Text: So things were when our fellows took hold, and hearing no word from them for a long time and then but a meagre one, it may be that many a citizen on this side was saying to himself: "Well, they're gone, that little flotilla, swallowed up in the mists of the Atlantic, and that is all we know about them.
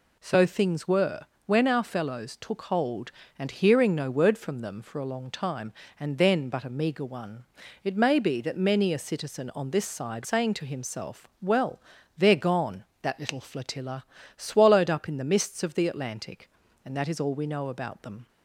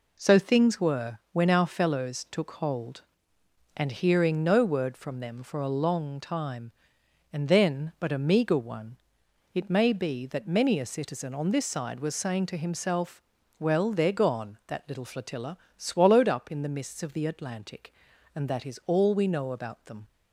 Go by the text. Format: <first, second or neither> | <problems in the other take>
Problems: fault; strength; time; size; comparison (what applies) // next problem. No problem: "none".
second | pauses between "were" and "when"; slight; at 1.2 s; 0.24 s long // skips "was"; at 10.2 s